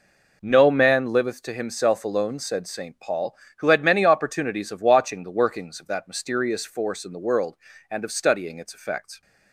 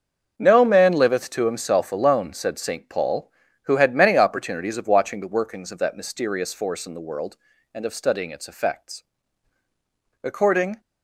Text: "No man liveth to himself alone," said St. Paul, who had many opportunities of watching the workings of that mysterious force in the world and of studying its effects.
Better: first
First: none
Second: starts louder than the rest; until 1.3 s; 6.5 dB // goes on to say "According"; from 10.2 s on; 0.56 s long

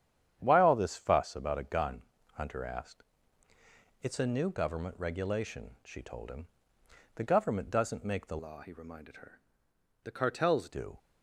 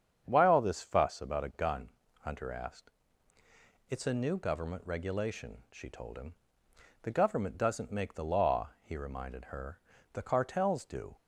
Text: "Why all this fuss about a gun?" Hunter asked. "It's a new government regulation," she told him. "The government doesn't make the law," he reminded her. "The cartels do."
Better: second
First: starts louder than the rest; strong; until 1.4 s; 9 dB // changes voice from "law" to "cartels"; from 8.3 to 10.6 s; 2.3 s long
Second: starts louder than the rest; strong; until 1.2 s; 7.5 dB

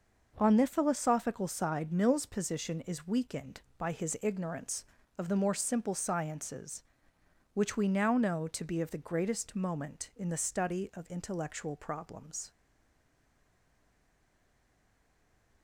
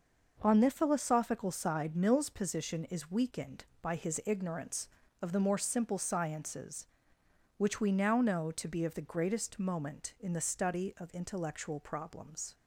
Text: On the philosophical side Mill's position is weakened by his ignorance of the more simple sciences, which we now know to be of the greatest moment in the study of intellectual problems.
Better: second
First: stays silent after the last word; strong; from 12.5 s on; 3.1 s long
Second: none

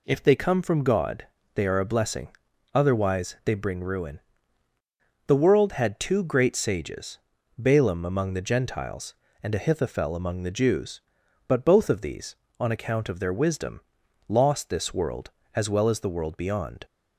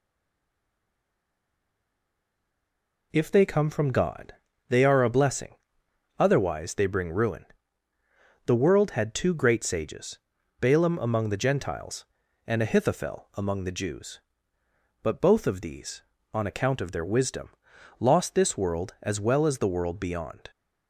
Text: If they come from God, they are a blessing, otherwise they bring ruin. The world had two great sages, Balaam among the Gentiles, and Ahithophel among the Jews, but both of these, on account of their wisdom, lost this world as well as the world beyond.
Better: first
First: none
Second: stays silent before the first word; strong; until 3.1 s; 3.1 s long

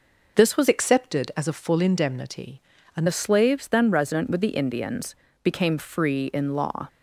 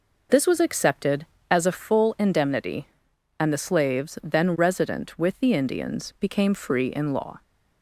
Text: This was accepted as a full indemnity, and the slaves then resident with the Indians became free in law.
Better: second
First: changes voice from "accepted" to "and"; from 0.6 to 3.0 s; 2.4 s long // pauses between "Indians" and "became"; slight; at 5.1 s; 0.30 s long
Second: none

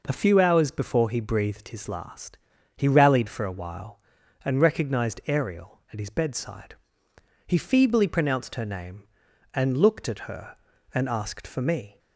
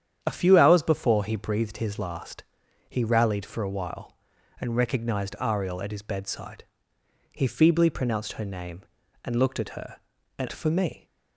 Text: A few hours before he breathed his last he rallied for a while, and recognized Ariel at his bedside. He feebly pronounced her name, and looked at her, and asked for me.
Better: first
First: pauses between "last" and "he"; at 2.3 s; 0.38 s long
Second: starts louder than the rest; strong; until 1.2 s; 9 dB // pauses between "last" and "he"; at 2.4 s; 0.44 s long // skips "asked"; at 10.5 s

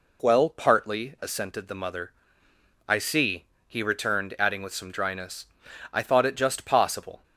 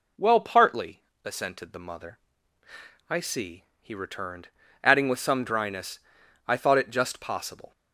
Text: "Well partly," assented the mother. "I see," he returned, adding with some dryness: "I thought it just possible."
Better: neither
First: none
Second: none

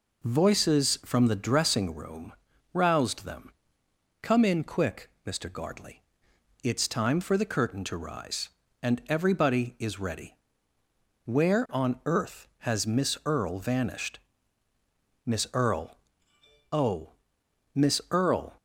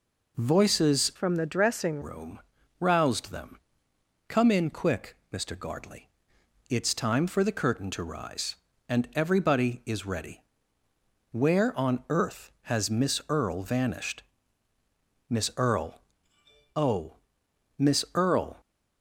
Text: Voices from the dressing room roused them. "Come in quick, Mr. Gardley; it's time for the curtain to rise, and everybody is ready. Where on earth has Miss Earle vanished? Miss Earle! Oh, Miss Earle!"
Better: first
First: pauses between "room" and "roused"; at 2.3 s; 0.40 s long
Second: changes voice from "from" to "dressing"; from 1.1 to 2.0 s; 0.9 s long // pauses between "room" and "roused"; at 2.3 s; 0.40 s long

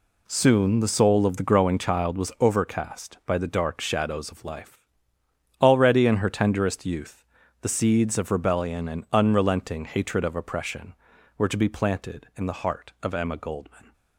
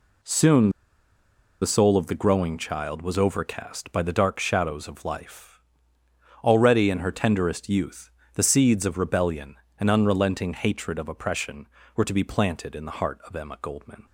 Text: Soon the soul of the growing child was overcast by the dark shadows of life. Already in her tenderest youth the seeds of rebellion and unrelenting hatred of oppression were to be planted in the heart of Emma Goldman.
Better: first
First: pauses between "youth" and "the"; slight; at 7.2 s; 0.36 s long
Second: pauses between "Soon" and "the"; noticeable; at 0.6 s; 0.91 s long // pauses between "youth" and "the"; slight; at 8.0 s; 0.26 s long

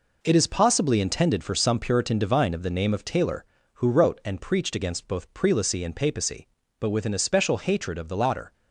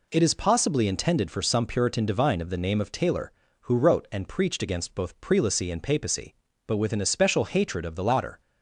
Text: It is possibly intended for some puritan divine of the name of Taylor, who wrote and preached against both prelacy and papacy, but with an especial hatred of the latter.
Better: second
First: gets quieter; strong; throughout; 7.5 dB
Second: none

